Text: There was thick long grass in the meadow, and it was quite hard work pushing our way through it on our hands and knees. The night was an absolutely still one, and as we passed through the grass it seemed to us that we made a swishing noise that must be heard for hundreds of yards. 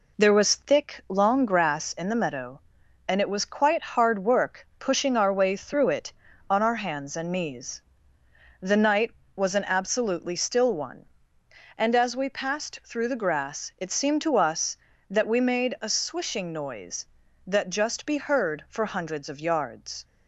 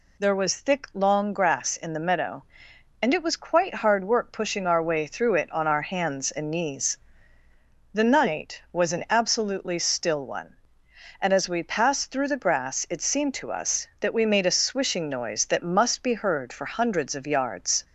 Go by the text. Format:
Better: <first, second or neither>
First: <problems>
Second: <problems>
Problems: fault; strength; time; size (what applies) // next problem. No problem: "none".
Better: second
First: says "just" for "must"; at 17.7 s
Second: none